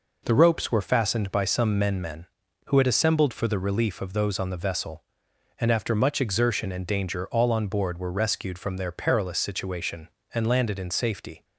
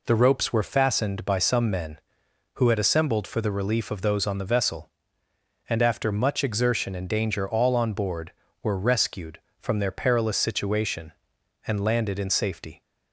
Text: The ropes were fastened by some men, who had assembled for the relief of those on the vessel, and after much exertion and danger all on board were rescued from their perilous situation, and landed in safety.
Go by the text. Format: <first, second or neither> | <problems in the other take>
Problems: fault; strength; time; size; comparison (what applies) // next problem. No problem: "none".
second | says "men" twice; at 2.0 s